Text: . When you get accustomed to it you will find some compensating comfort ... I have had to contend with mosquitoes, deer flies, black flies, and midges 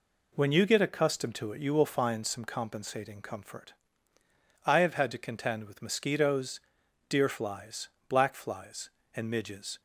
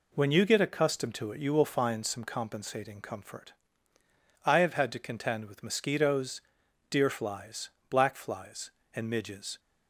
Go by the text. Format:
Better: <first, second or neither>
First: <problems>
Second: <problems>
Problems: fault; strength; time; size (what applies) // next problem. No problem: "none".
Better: neither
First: none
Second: none